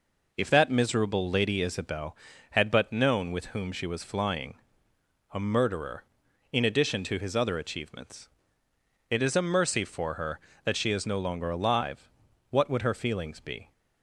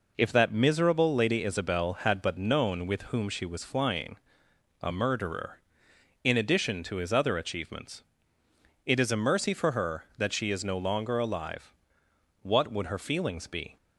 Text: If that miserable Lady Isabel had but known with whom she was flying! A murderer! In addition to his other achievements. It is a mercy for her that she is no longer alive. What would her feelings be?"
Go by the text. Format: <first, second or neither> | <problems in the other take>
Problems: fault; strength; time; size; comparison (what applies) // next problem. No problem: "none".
neither | none